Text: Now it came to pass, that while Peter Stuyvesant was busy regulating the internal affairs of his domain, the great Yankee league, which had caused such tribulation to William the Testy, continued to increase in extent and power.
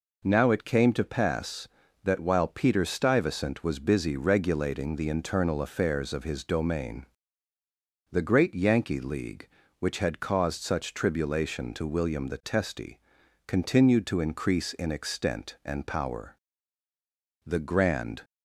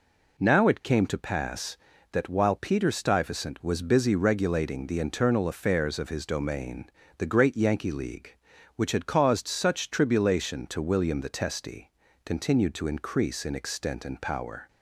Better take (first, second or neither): second